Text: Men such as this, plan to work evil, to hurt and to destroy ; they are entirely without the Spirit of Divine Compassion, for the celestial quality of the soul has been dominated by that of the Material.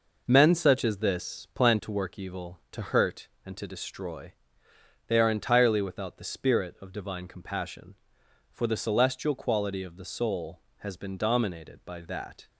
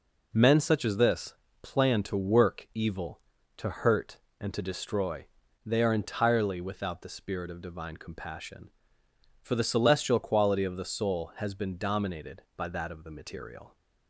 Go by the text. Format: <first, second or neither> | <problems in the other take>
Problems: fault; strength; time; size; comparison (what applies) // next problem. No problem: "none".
second | stops before "of the Material"; at 12.4 s